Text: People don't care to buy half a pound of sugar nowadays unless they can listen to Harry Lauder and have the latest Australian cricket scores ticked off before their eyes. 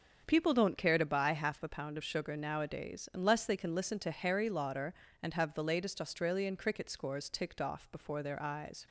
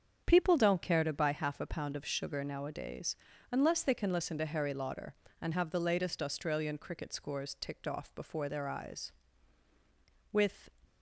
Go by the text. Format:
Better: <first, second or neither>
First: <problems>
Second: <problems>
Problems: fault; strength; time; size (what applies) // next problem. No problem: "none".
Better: first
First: starts louder than the rest; until 1.2 s; 7 dB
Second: starts louder than the rest; strong; until 1.2 s; 7 dB // pauses between "nowadays" and "unless"; slight; at 3.1 s; 0.36 s long // goes on to say "With"; slight; from 10.3 s on; 0.40 s long